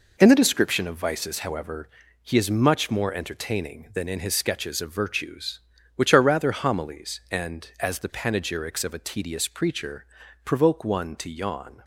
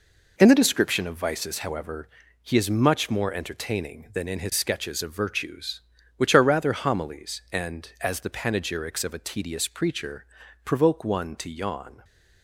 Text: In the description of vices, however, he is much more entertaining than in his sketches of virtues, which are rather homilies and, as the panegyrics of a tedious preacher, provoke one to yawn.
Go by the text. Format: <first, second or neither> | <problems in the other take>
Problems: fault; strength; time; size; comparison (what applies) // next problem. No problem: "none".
neither | none